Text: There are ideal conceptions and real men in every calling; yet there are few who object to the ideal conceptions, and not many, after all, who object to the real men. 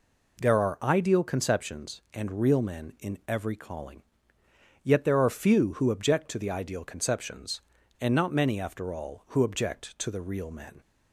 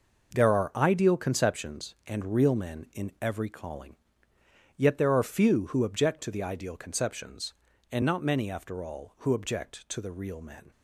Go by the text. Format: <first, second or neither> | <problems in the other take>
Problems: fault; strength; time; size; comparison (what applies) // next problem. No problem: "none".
first | gets quieter; strong; throughout; 10 dB